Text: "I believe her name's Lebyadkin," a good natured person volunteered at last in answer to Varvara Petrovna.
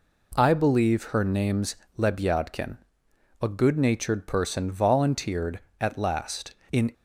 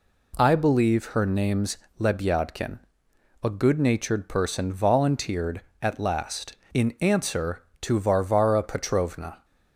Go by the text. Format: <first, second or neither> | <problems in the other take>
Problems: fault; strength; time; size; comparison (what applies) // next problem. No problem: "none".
second | pauses between "name's" and "Lebyadkin"; slight; at 1.7 s; 0.20 s long; slight in the second // stops before "answer to Varvara Petrovna"; at 6.9 s